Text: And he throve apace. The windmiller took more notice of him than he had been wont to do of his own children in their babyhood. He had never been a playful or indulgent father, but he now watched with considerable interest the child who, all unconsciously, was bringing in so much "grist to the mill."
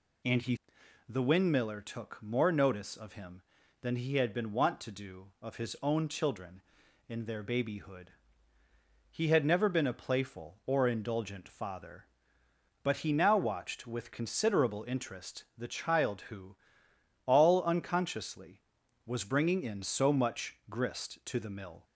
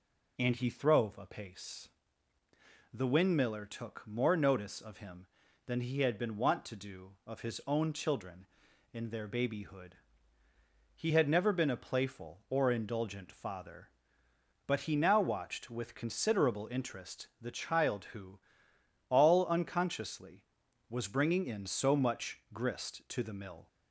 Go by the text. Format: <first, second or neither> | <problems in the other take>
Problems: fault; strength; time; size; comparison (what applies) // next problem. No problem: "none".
second | skips "throve apace"; at 0.8 s